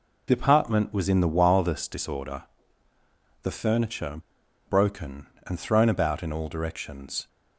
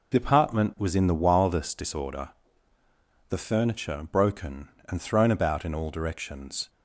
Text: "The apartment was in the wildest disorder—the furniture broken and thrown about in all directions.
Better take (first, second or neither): second